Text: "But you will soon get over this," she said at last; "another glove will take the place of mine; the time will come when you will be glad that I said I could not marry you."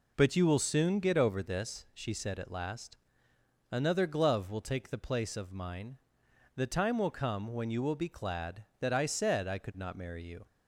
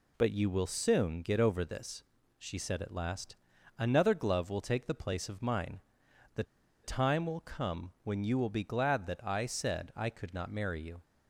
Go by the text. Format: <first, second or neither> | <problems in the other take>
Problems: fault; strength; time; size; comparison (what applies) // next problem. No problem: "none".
first | pauses between "the" and "time"; at 6.4 s; 0.39 s long